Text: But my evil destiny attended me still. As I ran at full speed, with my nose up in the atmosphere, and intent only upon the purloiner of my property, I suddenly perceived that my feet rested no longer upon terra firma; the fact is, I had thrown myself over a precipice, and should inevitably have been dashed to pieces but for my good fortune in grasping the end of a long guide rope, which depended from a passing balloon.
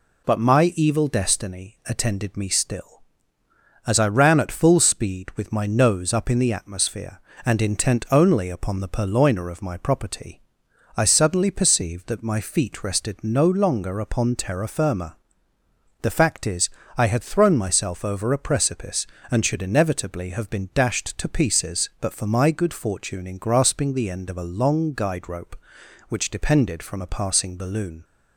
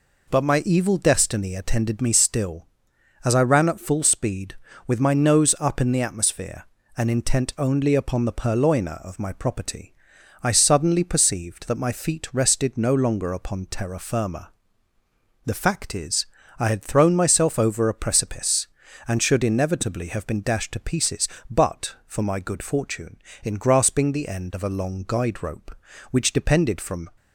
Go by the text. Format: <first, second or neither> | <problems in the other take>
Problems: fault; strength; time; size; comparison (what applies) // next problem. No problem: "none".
first | stops before "a passing balloon"; at 27.1 s